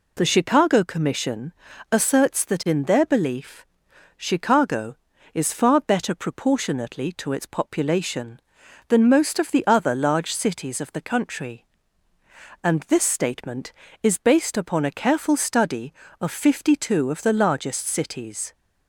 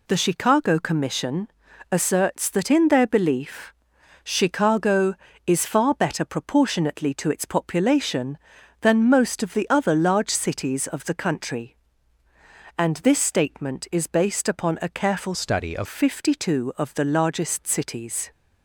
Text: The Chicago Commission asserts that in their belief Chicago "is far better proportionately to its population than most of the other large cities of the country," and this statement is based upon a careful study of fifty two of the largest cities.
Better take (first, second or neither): first